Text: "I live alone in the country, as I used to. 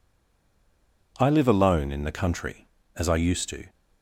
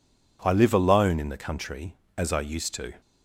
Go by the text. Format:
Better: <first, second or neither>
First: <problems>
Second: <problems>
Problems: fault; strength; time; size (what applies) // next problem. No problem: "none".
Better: second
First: stays silent before the first word; until 1.1 s; 1.1 s long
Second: none